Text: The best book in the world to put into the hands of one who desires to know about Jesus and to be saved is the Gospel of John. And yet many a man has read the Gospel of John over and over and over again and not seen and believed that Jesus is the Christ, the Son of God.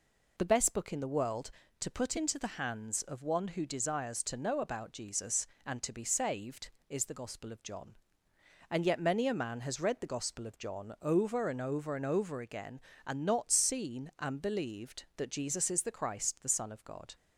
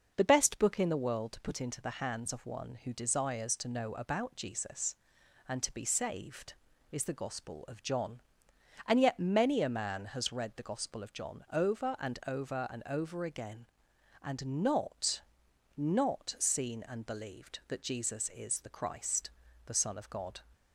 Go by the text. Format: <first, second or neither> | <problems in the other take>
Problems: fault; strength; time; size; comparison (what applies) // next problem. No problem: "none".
first | starts louder than the rest; noticeable; until 1.1 s; 6 dB // says "not" twice; at 15.7 s